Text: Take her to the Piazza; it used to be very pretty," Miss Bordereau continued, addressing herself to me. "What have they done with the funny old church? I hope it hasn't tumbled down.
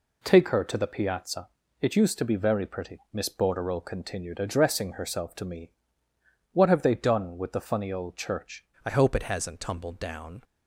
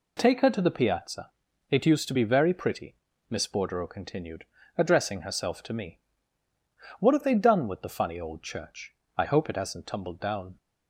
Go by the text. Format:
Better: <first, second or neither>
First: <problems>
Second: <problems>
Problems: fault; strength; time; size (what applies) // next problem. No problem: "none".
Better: second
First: changes voice at "I"; from 8.8 s on; 1.6 s long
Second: none